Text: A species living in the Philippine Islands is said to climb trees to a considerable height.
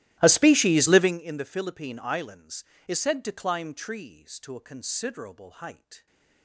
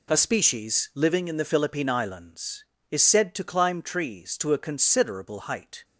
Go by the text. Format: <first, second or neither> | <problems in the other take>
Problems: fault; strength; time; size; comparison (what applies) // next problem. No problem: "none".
second | starts louder than the rest; strong; until 1.2 s; 15.5 dB